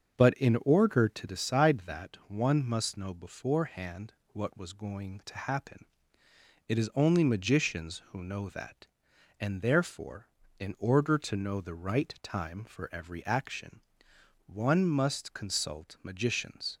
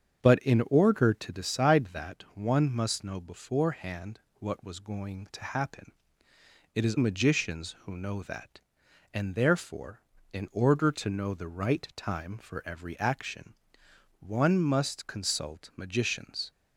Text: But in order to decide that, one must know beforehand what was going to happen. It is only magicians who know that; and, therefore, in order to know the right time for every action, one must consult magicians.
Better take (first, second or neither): first